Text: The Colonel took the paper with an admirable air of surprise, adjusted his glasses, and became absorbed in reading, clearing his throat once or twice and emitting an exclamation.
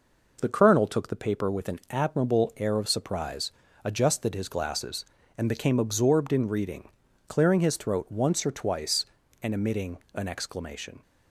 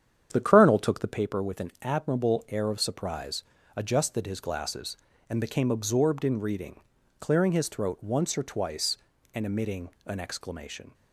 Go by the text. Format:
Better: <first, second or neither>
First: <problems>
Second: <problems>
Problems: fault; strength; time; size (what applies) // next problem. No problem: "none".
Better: first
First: pauses between "emitting" and "an"; slight; at 9.9 s; 0.16 s long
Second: starts louder than the rest; strong; until 1.2 s; 8.5 dB // pauses between "emitting" and "an"; slight; at 9.8 s; 0.16 s long